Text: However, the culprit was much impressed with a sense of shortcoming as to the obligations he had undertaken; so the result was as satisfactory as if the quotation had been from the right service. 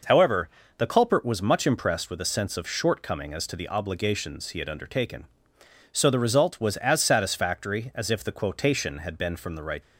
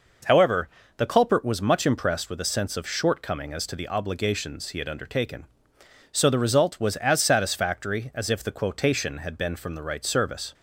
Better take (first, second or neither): second